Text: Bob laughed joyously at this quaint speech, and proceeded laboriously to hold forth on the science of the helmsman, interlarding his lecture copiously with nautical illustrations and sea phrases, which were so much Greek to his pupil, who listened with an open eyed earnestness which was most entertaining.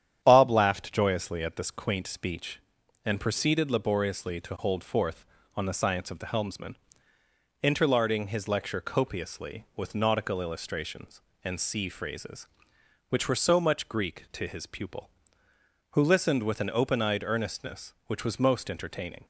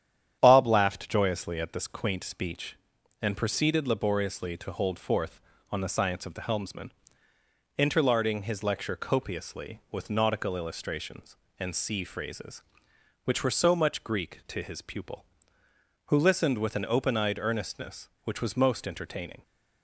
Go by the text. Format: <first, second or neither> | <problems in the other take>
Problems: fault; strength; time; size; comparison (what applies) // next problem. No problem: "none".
neither | starts louder than the rest; strong; the same in both